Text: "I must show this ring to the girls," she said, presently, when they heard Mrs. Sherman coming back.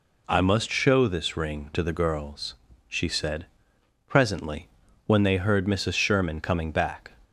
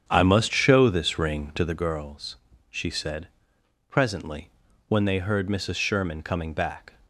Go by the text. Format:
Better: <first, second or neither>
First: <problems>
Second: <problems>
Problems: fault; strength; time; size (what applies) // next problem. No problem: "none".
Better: first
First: none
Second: starts louder than the rest; strong; until 1.8 s; 8.5 dB